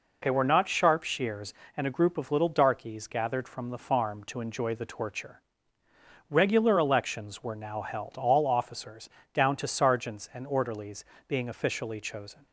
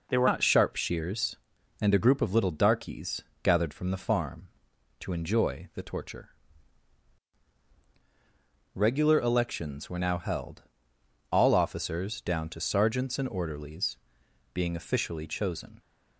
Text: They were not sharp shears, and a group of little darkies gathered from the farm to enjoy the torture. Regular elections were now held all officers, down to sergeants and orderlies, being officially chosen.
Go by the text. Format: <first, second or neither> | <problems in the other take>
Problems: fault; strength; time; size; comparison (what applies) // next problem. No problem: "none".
first | changes voice at "not"; from 0.2 s on; 15.5 s long // pauses between "darkies" and "gathered"; slight; at 3.2 s; 0.20 s long // pauses between "held" and "all"; noticeable; at 10.6 s; 0.68 s long